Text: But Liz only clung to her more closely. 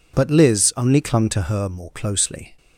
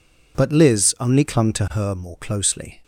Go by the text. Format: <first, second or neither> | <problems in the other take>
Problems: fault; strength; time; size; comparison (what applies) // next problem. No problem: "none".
neither | none